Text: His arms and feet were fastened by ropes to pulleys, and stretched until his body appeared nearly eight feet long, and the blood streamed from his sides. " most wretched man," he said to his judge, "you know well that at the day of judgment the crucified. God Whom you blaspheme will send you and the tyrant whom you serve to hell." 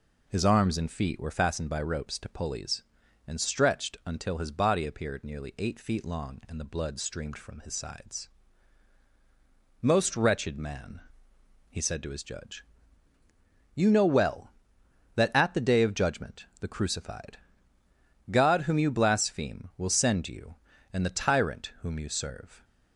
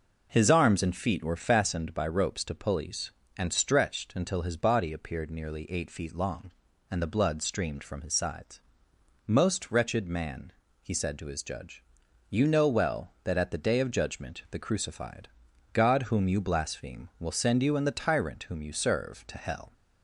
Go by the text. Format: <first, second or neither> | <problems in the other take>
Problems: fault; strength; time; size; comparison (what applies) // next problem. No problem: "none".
second | starts louder than the rest; until 1.2 s; 6.5 dB; also in the second // stops before "to hell"; at 22.6 s